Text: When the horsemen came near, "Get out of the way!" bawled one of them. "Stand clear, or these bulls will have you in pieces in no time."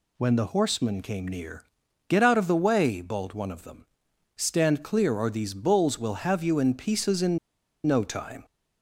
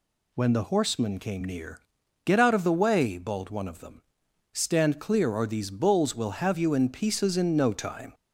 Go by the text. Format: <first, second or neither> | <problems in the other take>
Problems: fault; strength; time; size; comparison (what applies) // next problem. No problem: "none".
second | pauses between "in" and "no"; noticeable; at 7.3 s; 0.48 s long